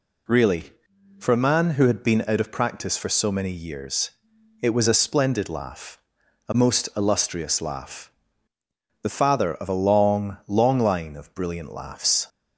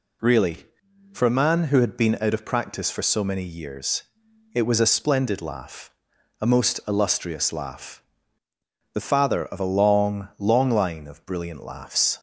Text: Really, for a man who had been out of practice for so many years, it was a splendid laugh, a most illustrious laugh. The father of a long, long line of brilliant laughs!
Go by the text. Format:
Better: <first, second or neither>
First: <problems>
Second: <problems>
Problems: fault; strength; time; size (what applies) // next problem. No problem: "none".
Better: neither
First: none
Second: none